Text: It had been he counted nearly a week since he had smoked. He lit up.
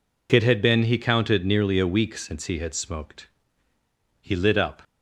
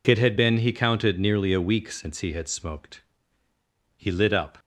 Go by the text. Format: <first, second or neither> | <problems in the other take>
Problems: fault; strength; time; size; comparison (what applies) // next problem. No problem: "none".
neither | none